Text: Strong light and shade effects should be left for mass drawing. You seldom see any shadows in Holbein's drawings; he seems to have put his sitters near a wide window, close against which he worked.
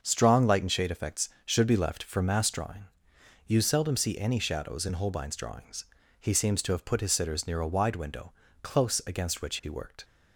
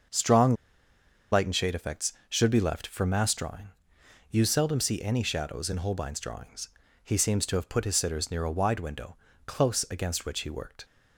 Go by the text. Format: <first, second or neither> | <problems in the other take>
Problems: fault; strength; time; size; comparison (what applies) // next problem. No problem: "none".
first | starts louder than the rest; until 1.8 s; 6.5 dB; also in the first // pauses between "Strong" and "light"; noticeable; at 0.5 s; 0.77 s long